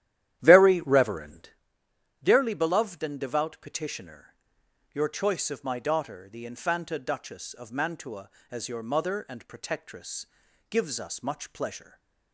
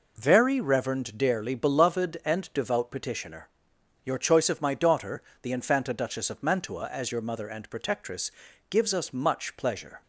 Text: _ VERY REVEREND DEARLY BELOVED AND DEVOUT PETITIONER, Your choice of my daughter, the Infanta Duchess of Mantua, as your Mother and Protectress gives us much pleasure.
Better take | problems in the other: second | starts louder than the rest; strong; until 1.5 s; 12 dB // pauses between "REVEREND" and "DEARLY"; noticeable; at 1.4 s; 0.74 s long // pauses between "Protectress" and "gives"; at 10.2 s; 0.42 s long; also in the second // stays silent after the last word; slight; from 11.8 s on; 0.5 s long

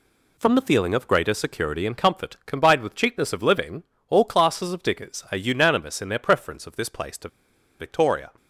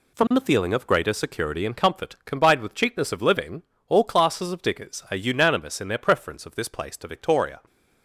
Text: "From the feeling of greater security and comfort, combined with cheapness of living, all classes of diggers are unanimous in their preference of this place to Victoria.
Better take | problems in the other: second | pauses between "to" and "Victoria"; noticeable; at 7.2 s; 0.51 s long

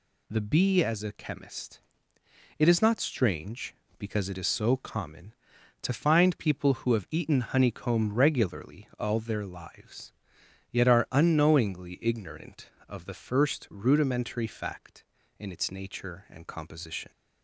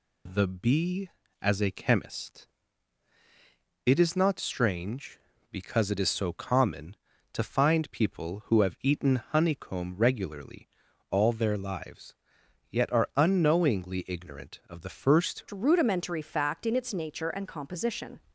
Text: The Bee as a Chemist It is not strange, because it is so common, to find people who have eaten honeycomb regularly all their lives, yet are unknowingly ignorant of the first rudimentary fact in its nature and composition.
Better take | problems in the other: first | pauses between "Chemist" and "It"; strong; at 2.4 s; 1.3 s long; noticeable in the first // pauses between "regularly" and "all"; at 10.6 s; 0.42 s long // changes voice at "rudimentary"; from 15.5 s on; 2.6 s long

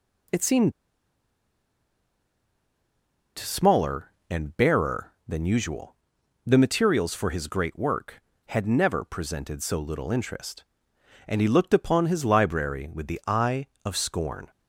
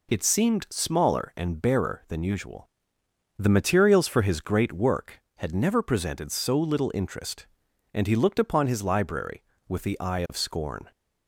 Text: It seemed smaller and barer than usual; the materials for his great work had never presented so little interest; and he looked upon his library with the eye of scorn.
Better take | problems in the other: second | pauses between "seemed" and "smaller"; strong; at 0.7 s; 2.6 s long

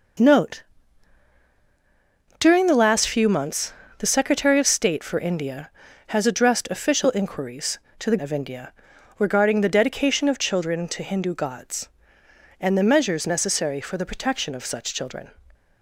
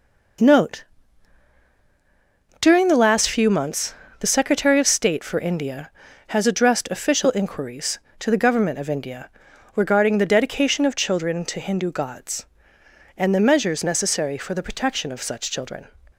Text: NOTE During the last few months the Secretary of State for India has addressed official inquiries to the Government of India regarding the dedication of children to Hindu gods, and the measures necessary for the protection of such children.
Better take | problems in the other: second | pauses between "NOTE" and "During"; strong; at 0.6 s; 1.7 s long; strong in the second // pauses between "months" and "the"; slight; at 3.7 s; 0.26 s long; slight in the second // skips "Government"; at 8.1 s // pauses between "India" and "regarding"; at 8.7 s; 0.44 s long; also in the second

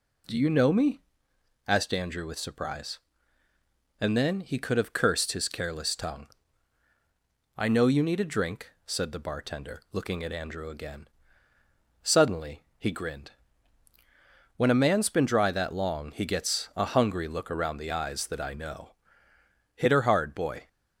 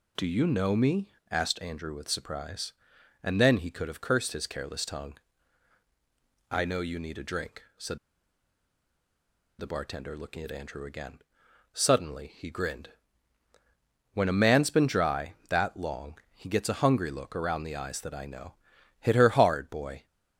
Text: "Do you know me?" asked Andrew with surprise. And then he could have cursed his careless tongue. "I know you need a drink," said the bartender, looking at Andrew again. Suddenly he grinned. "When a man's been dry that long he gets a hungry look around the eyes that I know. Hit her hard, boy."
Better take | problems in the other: first | pauses between "said" and "the"; strong; at 7.9 s; 1.6 s long // pauses between "long" and "he"; slight; at 16.1 s; 0.16 s long

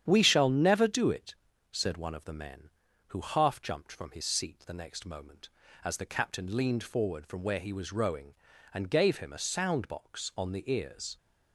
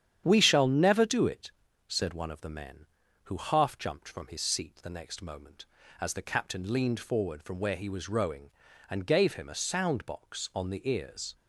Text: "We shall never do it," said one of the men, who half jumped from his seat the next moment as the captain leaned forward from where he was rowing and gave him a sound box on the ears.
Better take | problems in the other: neither | starts louder than the rest; strong; the same in both

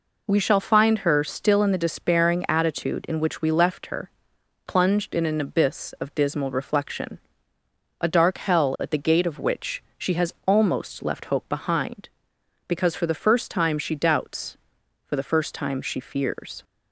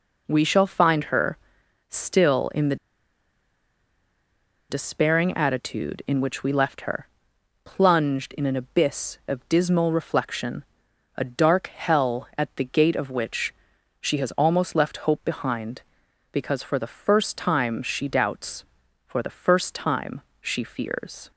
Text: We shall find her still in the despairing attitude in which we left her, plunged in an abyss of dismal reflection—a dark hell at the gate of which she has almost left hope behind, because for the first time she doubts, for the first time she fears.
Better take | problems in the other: first | pauses between "her" and "still"; noticeable; at 1.3 s; 0.52 s long // pauses between "the" and "despairing"; strong; at 2.7 s; 1.9 s long // pauses between "which" and "she"; noticeable; at 13.5 s; 0.48 s long // pauses between "time" and "she"; slight; at 20.2 s; 0.20 s long

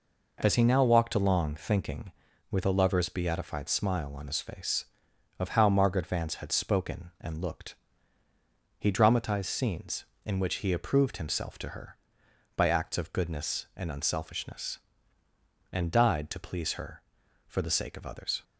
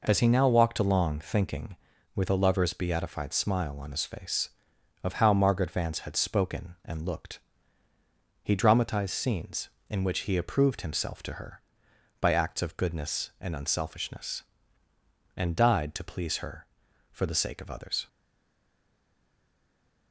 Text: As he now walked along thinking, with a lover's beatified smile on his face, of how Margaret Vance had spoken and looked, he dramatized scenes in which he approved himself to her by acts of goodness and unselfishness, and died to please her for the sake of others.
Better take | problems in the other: first | stays silent after the last word; noticeable; from 18.0 s on; 2.1 s long

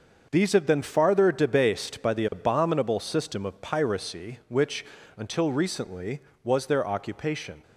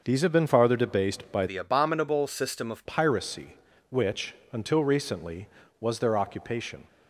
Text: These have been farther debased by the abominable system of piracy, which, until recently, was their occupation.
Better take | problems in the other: first | starts louder than the rest; noticeable; until 1.0 s; 6 dB; also in the first // changes voice from "the" to "of"; from 1.4 to 2.8 s; 1.4 s long

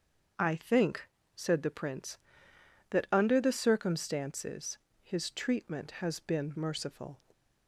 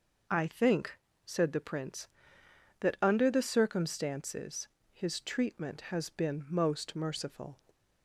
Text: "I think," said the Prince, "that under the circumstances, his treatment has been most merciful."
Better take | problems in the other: second | starts louder than the rest; until 1.6 s; 7 dB // skips "most"; at 6.5 s

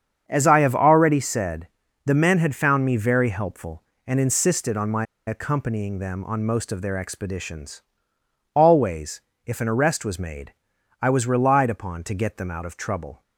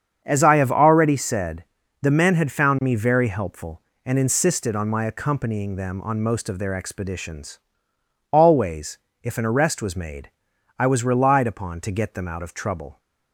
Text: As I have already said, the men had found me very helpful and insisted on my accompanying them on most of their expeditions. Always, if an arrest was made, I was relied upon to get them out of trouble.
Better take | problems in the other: second | starts louder than the rest; strong; until 1.2 s; 7.5 dB; strong in the second // pauses between "my" and "accompanying"; slight; at 5.0 s; 0.22 s long

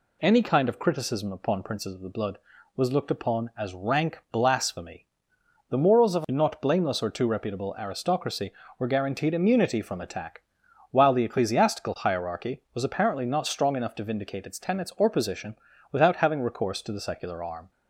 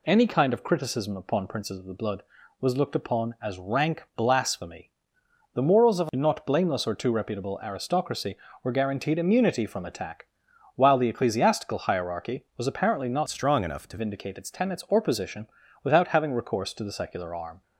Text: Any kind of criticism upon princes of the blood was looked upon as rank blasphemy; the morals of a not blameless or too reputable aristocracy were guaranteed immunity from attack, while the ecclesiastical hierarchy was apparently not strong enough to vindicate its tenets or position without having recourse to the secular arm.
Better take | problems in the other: first | changes voice from "strong" to "to"; from 13.2 to 13.9 s; 0.7 s long // pauses between "position" and "without"; slight; at 15.4 s; 0.34 s long; slight in the first

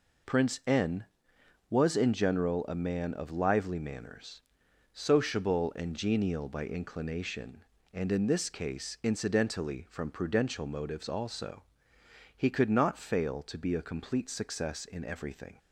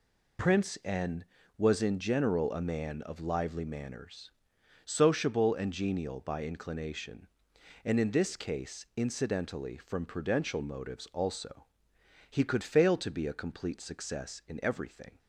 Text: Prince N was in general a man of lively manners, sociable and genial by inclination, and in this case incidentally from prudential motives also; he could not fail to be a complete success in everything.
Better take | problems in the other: first | skips "not"; at 12.6 s

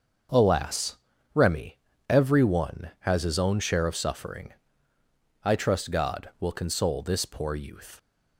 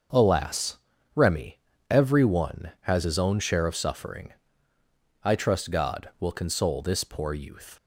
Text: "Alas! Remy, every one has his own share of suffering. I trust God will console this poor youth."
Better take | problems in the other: neither | starts louder than the rest; the same in both

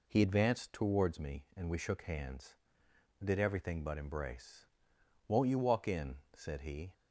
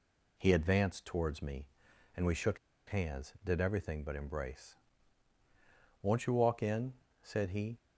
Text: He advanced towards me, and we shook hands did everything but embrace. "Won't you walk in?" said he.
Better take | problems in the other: first | pauses between "shook" and "hands"; slight; at 2.5 s; 0.31 s long

